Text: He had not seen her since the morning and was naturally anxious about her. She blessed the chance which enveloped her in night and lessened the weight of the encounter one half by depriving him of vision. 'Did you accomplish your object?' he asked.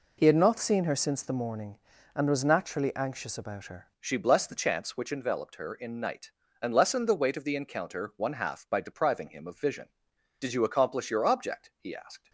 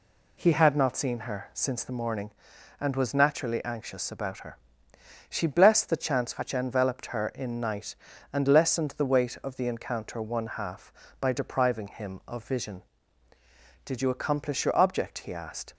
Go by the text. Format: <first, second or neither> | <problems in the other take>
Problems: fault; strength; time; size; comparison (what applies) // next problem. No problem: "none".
second | changes voice at "She"; from 3.9 s on; 8.3 s long